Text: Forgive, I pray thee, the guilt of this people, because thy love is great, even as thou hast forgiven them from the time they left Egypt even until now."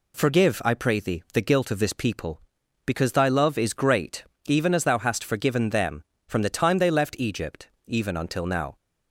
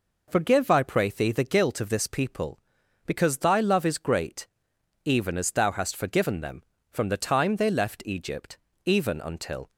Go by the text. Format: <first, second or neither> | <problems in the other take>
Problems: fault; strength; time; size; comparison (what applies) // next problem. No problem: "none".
first | pauses between "Egypt" and "even"; slight; at 8.5 s; 0.26 s long; slight in the first // stops before "now"; at 9.7 s